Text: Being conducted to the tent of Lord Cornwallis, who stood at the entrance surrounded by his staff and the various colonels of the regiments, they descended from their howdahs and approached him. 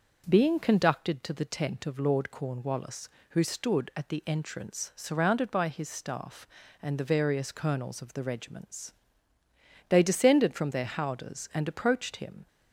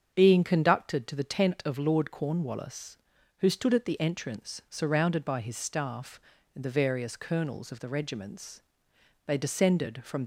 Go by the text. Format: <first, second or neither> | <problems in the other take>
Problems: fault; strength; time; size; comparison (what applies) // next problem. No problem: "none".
first | starts louder than the rest; strong; until 1.1 s; 7.5 dB; also in the first // stops before "their howdahs and approached him"; at 10.2 s